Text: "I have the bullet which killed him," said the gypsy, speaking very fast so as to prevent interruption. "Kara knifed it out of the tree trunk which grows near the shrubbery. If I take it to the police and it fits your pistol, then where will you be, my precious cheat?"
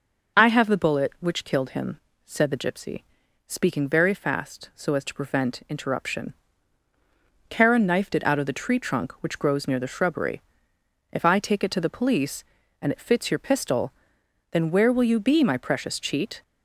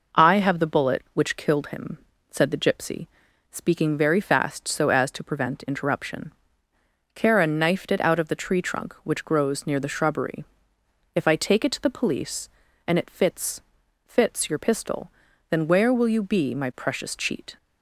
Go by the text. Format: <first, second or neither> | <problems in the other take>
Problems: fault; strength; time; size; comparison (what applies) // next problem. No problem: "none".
first | says "fits" twice; at 14.0 s